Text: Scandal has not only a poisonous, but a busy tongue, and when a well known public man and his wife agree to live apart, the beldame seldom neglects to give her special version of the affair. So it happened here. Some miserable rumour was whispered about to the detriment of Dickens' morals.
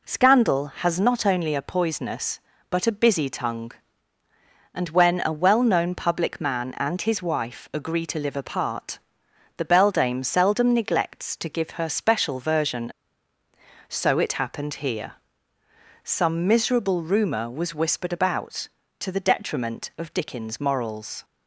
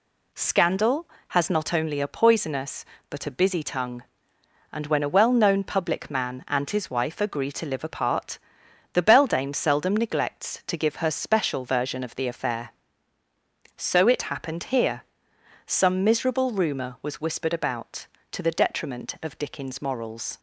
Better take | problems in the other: second | skips "of the affair"; at 13.3 s

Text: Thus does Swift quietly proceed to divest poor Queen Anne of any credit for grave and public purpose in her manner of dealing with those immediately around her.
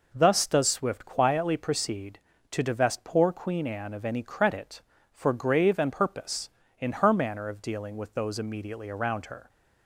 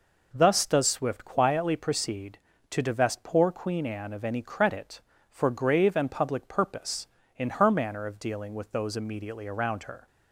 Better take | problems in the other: second | skips "public"; at 5.9 s

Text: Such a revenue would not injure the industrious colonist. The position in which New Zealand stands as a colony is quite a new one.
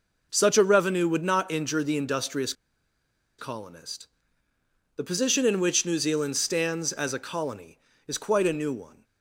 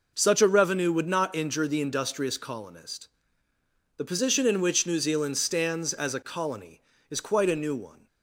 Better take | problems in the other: second | pauses between "industrious" and "colonist"; noticeable; at 2.5 s; 0.86 s long

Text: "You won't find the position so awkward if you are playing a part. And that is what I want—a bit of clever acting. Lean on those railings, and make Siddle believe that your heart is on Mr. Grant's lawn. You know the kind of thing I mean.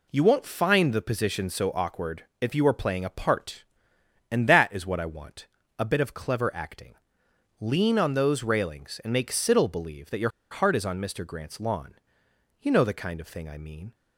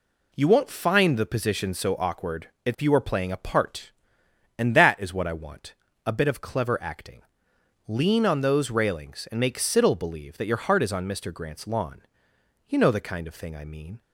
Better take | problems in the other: second | pauses between "awkward" and "if"; slight; at 2.2 s; 0.16 s long; slight in the second // pauses between "your" and "heart"; slight; at 10.2 s; 0.21 s long

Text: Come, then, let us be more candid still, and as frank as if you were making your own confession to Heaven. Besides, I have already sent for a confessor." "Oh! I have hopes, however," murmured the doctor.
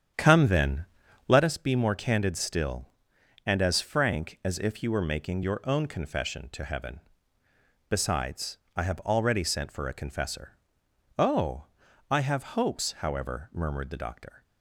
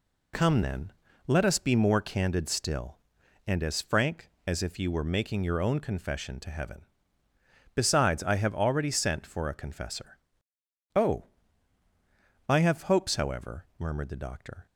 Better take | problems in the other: second | starts louder than the rest; strong; until 1.5 s; 9 dB

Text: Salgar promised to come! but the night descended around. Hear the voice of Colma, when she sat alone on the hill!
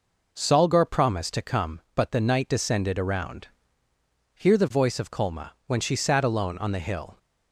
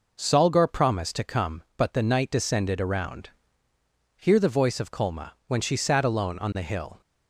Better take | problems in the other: neither | none

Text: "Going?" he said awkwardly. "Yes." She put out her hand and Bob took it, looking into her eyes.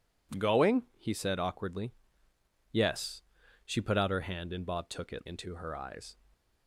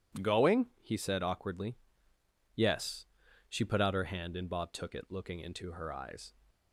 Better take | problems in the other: second | skips "looking"; at 5.2 s

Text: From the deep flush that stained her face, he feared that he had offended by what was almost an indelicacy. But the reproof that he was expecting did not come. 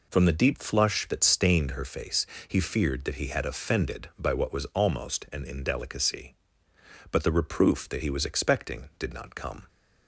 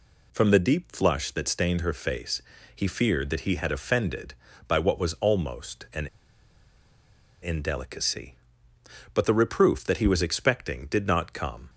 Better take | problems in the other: first | pauses between "an" and "indelicacy"; strong; at 6.0 s; 1.3 s long

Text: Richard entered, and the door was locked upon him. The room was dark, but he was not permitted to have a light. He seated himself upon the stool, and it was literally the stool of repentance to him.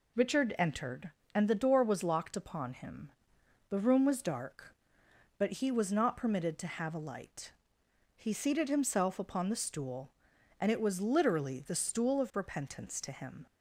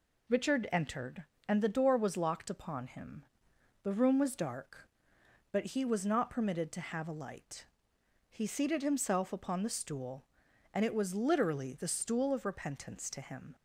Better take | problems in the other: neither | none

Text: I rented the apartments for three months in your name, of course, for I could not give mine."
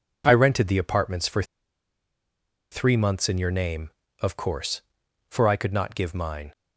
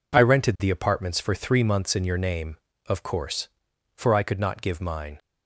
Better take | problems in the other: second | pauses between "for" and "three"; strong; at 1.4 s; 1.2 s long

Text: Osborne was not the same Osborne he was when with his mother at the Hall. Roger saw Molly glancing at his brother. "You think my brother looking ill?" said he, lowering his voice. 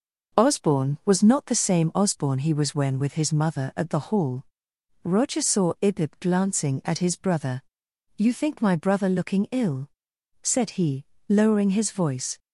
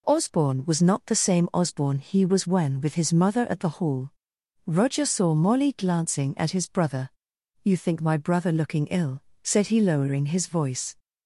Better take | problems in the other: second | says "Ibib" for "Molly"; at 5.8 s

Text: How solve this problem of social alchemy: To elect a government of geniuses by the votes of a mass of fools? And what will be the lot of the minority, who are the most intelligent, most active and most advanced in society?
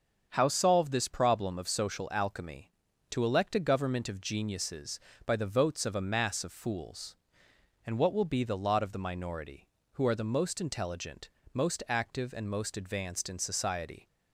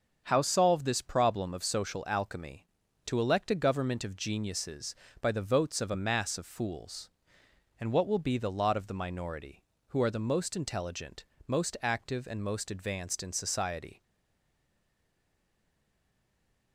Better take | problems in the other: first | starts louder than the rest; until 1.2 s; 7 dB; strong in the first // stays silent after the last word; strong; from 14.0 s on; 2.7 s long

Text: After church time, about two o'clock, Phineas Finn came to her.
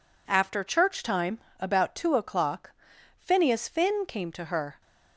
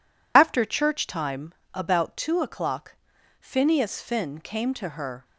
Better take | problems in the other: first | loses the start of "After"; at 0.3 s; 70 ms

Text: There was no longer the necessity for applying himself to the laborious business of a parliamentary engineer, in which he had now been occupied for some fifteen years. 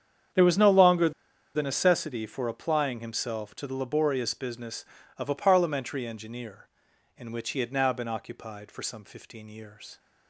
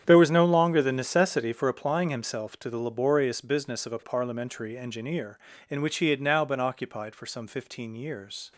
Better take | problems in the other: second | starts louder than the rest; strong; until 1.7 s; 8.5 dB; strong in the second // pauses between "longer" and "the"; at 1.1 s; 0.44 s long

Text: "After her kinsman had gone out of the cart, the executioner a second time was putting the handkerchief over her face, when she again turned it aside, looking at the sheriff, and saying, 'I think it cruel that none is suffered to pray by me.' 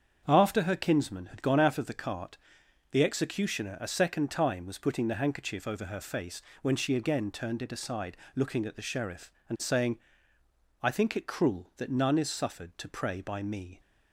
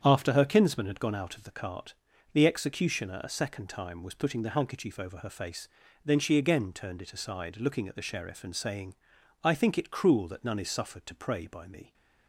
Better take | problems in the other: first | starts louder than the rest; strong; until 1.0 s; 8.5 dB; strong in the first // says "then" for "when"; at 6.0 s

